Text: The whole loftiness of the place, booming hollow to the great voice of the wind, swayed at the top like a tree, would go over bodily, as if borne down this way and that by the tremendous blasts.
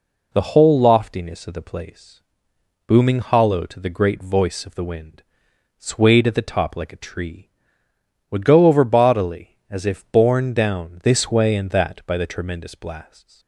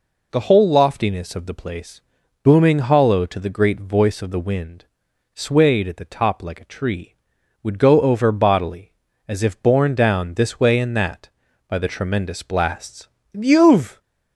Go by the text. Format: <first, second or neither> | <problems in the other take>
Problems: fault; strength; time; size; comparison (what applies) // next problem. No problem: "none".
first | goes on to say "You've"; noticeable; from 13.3 s on; 0.68 s long